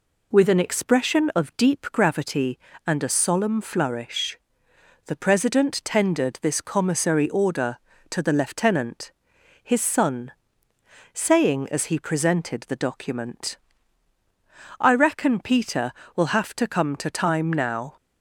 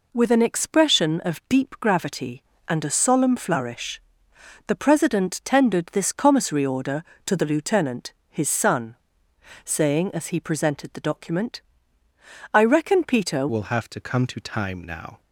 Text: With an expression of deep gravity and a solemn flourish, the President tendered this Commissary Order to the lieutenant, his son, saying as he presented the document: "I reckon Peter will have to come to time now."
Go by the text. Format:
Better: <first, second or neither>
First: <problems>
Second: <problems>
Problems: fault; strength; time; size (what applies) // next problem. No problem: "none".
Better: first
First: none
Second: changes voice at "will"; from 13.4 s on; 1.8 s long